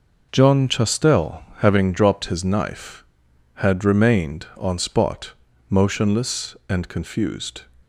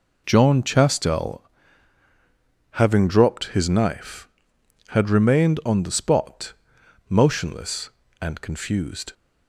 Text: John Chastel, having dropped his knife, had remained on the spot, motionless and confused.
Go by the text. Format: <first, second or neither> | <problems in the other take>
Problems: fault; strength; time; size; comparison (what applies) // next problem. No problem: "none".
second | skips "the"; at 4.7 s